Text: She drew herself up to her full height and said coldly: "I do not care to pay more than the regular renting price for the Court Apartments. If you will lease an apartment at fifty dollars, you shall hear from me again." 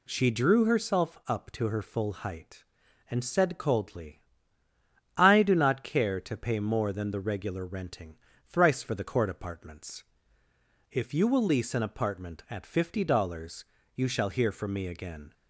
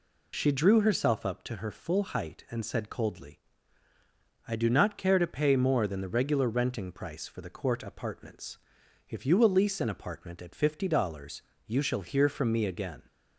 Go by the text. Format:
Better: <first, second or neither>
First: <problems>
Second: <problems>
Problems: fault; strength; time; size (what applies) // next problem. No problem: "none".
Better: second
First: says "thrice" for "price"; at 8.4 s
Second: none